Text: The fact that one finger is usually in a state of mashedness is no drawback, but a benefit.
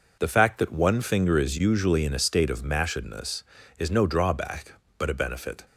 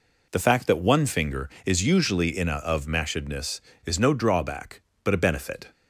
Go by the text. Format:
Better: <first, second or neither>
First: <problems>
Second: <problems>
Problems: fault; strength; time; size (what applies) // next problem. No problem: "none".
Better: first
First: none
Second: skips "state"; at 2.5 s